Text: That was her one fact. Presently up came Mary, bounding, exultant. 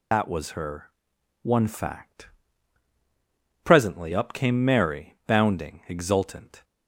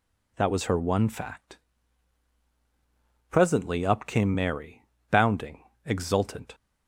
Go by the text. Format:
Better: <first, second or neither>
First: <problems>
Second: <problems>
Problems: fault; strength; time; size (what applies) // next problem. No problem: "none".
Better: second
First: loses the start of "That"; at 0.1 s; 40 ms // pauses between "her" and "one"; noticeable; at 0.8 s; 0.54 s long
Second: none